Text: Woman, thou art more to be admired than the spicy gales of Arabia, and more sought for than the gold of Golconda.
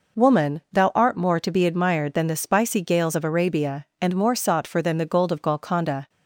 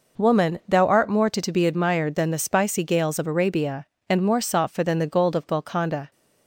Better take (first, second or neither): first